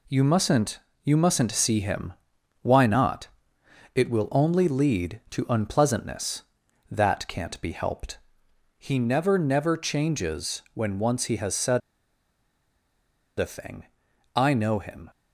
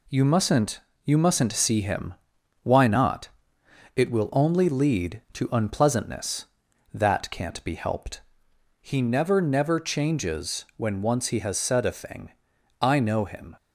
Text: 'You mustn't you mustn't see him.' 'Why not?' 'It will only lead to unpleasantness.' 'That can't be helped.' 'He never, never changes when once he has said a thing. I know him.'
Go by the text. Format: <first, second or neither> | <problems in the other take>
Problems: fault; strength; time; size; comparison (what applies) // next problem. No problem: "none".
second | pauses between "mustn't" and "you"; slight; at 0.7 s; 0.24 s long; slight in the second // pauses between "said" and "a"; strong; at 11.8 s; 1.5 s long